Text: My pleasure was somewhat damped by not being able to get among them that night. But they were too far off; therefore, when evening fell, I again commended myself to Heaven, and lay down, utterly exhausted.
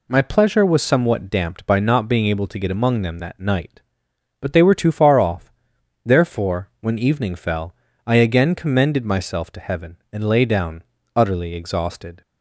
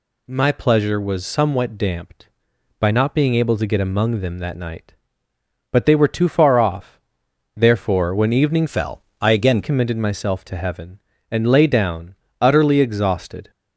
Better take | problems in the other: first | changes voice from "fell" to "again"; from 8.6 to 9.6 s; 1.0 s long

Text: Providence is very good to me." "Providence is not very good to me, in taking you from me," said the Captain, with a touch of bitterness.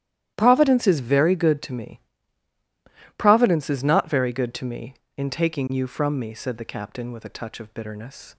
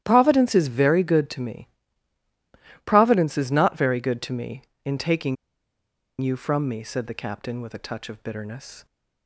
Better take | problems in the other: first | starts louder than the rest; strong; until 1.0 s; 12 dB; strong in the first // pauses between "taking" and "you"; noticeable; at 5.3 s; 0.85 s long

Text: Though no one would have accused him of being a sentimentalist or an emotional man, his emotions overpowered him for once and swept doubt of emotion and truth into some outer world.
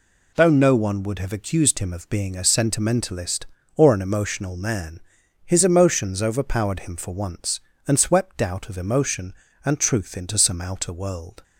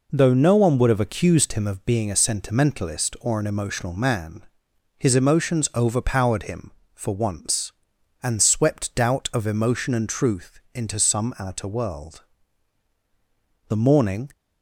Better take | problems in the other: first | pauses between "truth" and "into"; slight; at 10.5 s; 0.16 s long // goes on to say "The morning"; noticeable; from 13.6 s on; 0.62 s long

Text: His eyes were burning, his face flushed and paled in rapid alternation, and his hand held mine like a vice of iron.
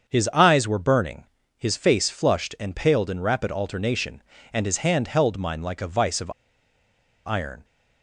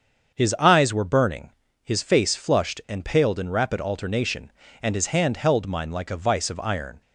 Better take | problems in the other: second | starts louder than the rest; until 1.1 s; 7 dB; also in the second // pauses between "of" and "iron"; noticeable; at 6.3 s; 0.94 s long

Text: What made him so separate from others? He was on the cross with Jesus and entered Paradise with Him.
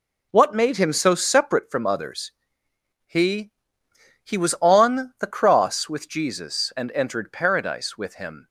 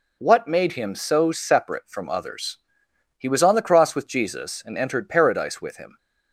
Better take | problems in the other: second | says "He" twice; at 4.2 s

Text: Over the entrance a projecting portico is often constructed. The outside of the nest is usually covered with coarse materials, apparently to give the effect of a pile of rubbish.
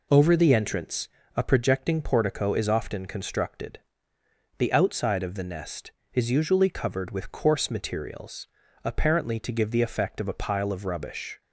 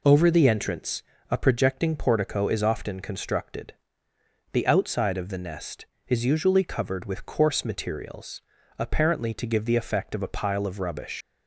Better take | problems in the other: first | pauses between "entrance" and "a"; slight; at 1.0 s; 0.26 s long; slight in the first // leaves "rubbish" unfinished; at 11.2 s; 140 ms

